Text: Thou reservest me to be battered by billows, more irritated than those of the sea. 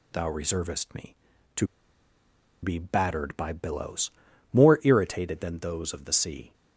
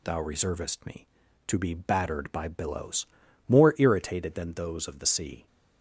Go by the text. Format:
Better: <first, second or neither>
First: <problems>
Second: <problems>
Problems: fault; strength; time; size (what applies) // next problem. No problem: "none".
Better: second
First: pauses between "to" and "be"; noticeable; at 1.6 s; 0.97 s long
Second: none